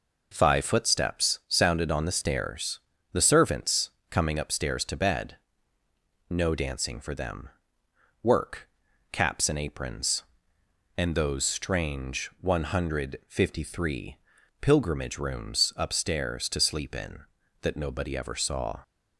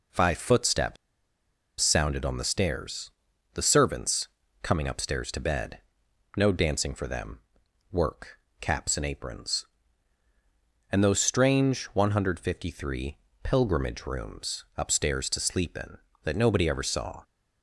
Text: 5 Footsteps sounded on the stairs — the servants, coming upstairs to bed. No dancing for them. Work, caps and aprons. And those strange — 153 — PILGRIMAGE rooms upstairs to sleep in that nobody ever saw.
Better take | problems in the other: first | pauses between "Footsteps" and "sounded"; noticeable; at 0.9 s; 0.84 s long

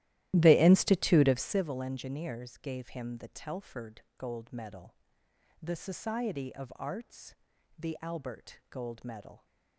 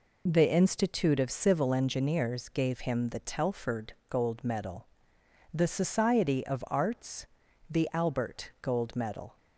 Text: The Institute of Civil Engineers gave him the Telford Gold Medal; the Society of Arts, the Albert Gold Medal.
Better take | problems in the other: second | starts louder than the rest; strong; until 1.7 s; 14 dB // pauses between "Telford" and "Gold"; slight; at 4.0 s; 0.16 s long; slight in the second

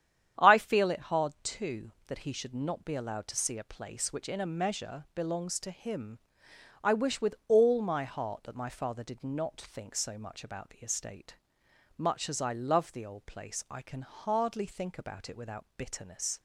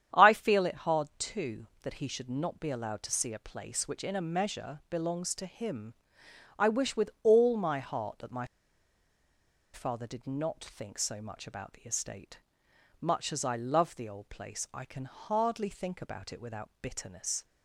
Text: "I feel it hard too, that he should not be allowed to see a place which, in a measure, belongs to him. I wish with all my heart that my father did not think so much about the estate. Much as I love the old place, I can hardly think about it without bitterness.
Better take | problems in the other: first | starts louder than the rest; strong; until 1.2 s; 9.5 dB; strong in the first // pauses between "my" and "father"; strong; at 8.4 s; 1.2 s long

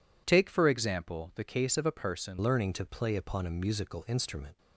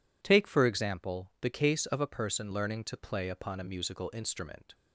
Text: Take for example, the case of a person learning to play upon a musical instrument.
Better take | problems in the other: second | changes voice at "learning"; from 2.4 s on; 2.1 s long

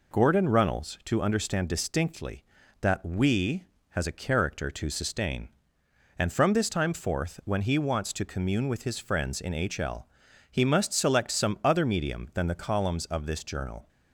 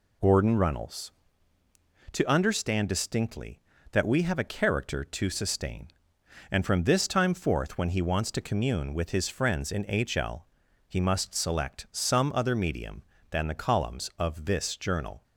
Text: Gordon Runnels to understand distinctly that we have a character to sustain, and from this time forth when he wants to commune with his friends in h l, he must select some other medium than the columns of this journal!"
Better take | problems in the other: second | says "has" for "have"; at 3.8 s

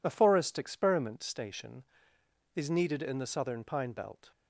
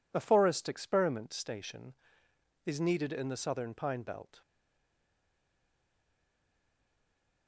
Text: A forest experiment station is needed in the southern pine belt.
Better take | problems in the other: first | stays silent after the last word; strong; from 4.4 s on; 3.0 s long

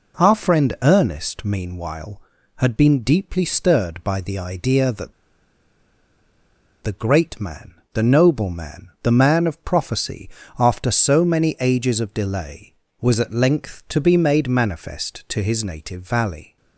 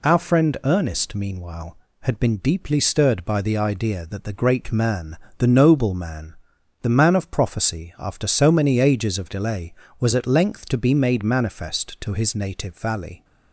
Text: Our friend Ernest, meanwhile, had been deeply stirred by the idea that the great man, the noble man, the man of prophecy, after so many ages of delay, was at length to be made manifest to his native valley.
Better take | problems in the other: second | pauses between "that" and "the"; strong; at 5.1 s; 1.7 s long

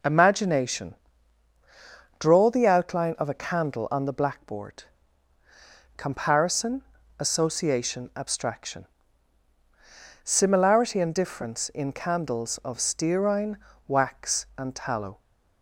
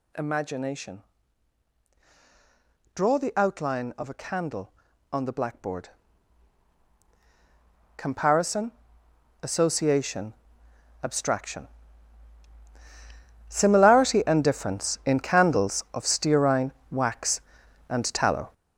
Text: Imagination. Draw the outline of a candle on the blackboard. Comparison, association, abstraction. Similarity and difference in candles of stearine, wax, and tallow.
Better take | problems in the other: first | gets louder; strong; throughout; 8.5 dB

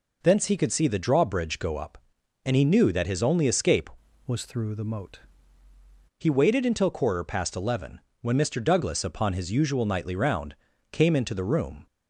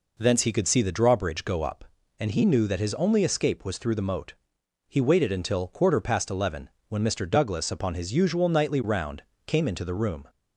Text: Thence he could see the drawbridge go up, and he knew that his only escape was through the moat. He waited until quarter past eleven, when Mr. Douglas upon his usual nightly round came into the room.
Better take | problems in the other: second | changes voice from "was" to "moat"; from 4.2 to 5.1 s; 0.9 s long // pauses between "round" and "came"; at 10.5 s; 0.38 s long; slight in the second

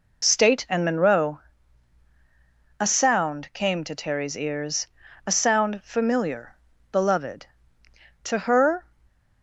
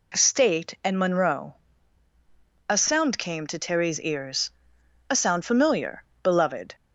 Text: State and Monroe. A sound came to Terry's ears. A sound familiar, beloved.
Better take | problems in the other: second | goes on to say "To her"; noticeable; from 8.2 s on; 0.62 s long

